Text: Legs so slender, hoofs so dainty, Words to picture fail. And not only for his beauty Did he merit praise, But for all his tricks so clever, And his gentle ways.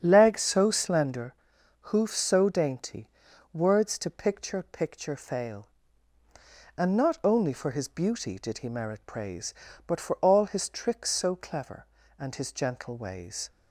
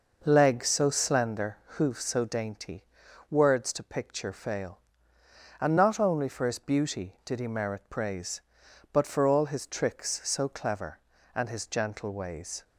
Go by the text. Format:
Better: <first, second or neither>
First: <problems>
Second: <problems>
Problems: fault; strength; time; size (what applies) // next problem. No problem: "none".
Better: second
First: starts louder than the rest; strong; until 1.0 s; 8 dB // says "picture" twice; at 4.6 s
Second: none